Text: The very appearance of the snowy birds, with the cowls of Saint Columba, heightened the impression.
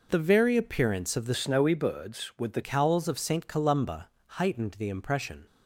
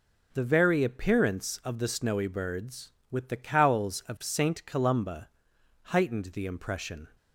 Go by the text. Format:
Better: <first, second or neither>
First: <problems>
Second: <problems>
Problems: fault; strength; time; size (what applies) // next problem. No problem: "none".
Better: second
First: changes voice from "snowy" to "the"; from 1.3 to 2.6 s; 1.3 s long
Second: none